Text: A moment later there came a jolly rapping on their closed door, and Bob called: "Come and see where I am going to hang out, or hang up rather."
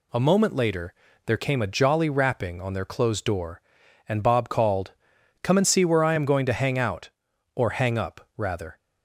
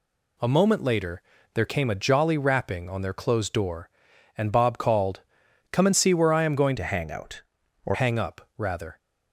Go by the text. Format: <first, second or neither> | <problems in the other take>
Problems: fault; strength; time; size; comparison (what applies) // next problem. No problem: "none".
first | pauses between "later" and "there"; slight; at 1.2 s; 0.32 s long; slight in the first // changes voice from "to" to "or"; from 6.7 to 7.9 s; 1.2 s long